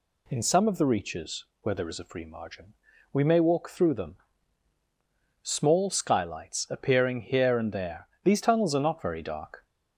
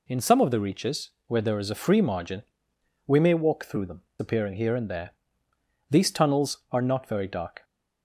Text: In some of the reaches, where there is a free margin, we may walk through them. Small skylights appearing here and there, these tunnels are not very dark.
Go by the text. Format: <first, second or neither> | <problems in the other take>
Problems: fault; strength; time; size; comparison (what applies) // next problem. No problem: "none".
first | skips "Small skylights"; at 4.1 s